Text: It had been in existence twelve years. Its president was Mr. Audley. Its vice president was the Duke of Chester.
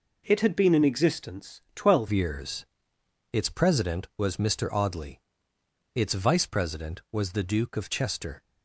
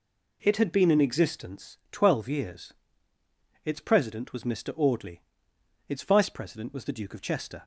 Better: second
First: changes voice at "years"; from 2.1 s on; 6.3 s long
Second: none

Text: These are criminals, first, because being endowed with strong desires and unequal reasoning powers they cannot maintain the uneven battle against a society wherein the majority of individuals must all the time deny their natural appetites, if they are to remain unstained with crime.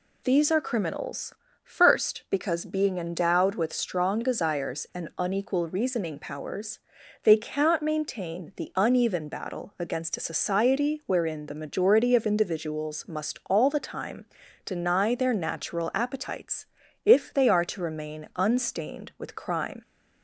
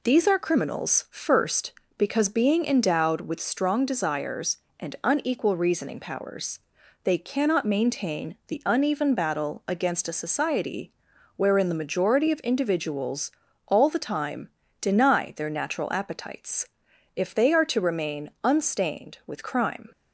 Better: first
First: pauses between "powers" and "they"; at 6.7 s; 0.44 s long // pauses between "time" and "deny"; at 14.2 s; 0.40 s long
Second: pauses between "powers" and "they"; at 6.5 s; 0.44 s long // pauses between "society" and "wherein"; at 10.9 s; 0.44 s long // skips "must"; at 13.4 s // pauses between "time" and "deny"; slight; at 14.4 s; 0.32 s long

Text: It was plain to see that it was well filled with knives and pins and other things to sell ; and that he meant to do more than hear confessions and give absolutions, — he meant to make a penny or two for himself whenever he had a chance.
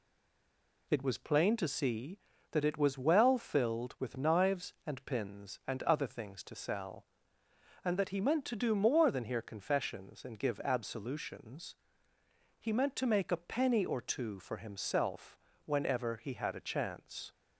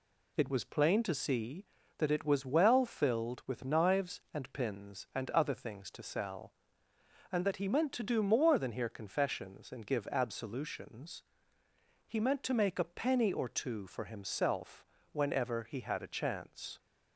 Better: second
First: stays silent before the first word; slight; until 0.8 s; 0.8 s long // pauses between "himself" and "whenever"; slight; at 15.3 s; 0.26 s long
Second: pauses between "himself" and "whenever"; slight; at 14.8 s; 0.25 s long

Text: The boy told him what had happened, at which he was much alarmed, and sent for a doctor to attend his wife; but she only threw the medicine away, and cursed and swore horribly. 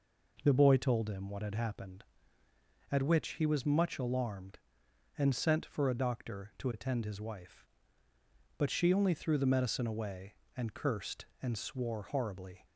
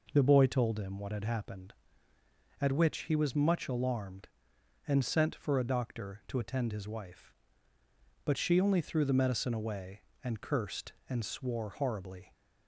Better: neither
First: none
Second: none

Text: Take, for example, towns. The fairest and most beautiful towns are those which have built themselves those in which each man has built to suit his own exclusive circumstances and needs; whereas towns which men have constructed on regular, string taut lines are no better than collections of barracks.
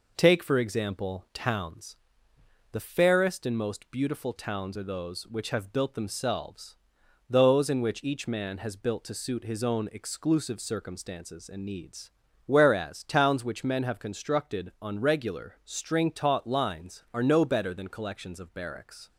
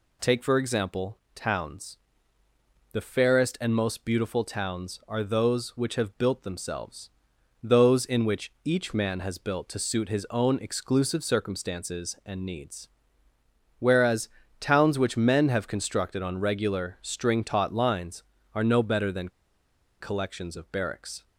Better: first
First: pauses between "themselves" and "those"; noticeable; at 6.7 s; 0.50 s long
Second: pauses between "themselves" and "those"; noticeable; at 7.1 s; 0.52 s long // pauses between "whereas" and "towns"; slight; at 14.2 s; 0.32 s long // pauses between "than" and "collections"; noticeable; at 19.2 s; 0.71 s long

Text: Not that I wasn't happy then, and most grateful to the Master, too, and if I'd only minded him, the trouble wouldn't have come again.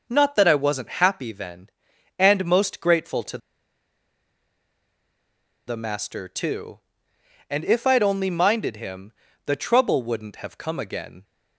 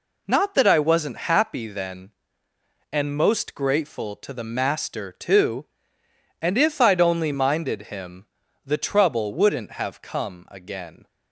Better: second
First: pauses between "to" and "the"; strong; at 3.3 s; 2.2 s long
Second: none

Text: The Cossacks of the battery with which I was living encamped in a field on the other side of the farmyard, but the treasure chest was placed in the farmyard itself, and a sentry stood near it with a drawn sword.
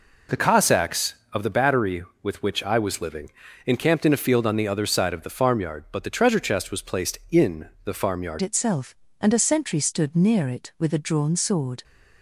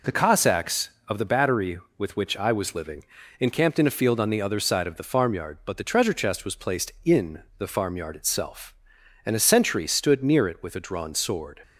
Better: second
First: pauses between "living" and "encamped"; slight; at 3.2 s; 0.36 s long // pauses between "in" and "the"; slight; at 7.6 s; 0.16 s long // changes voice at "itself"; from 8.4 s on; 3.4 s long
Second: pauses between "living" and "encamped"; slight; at 3.0 s; 0.36 s long // pauses between "in" and "the"; slight; at 7.4 s; 0.16 s long

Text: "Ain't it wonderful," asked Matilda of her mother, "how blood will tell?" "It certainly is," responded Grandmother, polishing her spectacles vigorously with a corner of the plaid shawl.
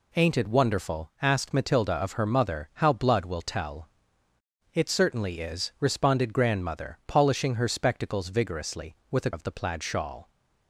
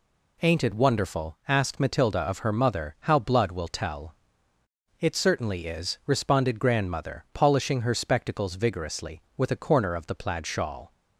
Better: second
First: skips "corner"; at 9.3 s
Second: none

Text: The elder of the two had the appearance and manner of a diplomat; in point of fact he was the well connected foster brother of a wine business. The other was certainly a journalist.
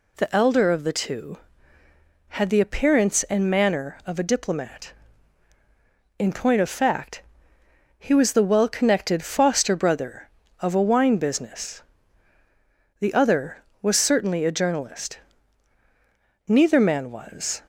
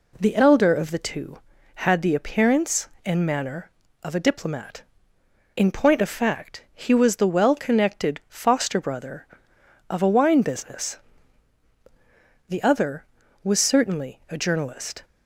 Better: second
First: pauses between "fact" and "he"; noticeable; at 7.2 s; 0.78 s long // goes on to say "Neither man was"; noticeable; from 16.4 s on; 1.1 s long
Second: none

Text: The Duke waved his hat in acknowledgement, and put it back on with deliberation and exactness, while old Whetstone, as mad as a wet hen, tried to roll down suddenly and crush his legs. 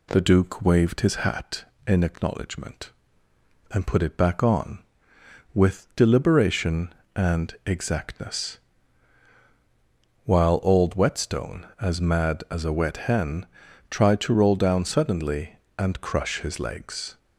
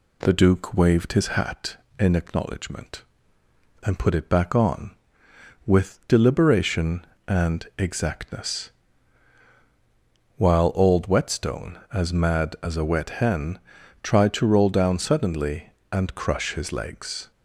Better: neither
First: none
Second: none

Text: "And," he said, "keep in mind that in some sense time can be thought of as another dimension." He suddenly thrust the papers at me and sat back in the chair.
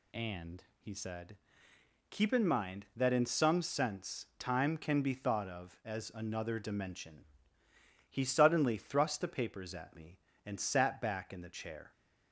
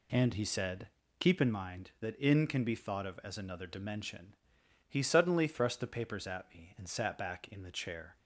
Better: first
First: none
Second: skips "some sense time"; at 2.4 s

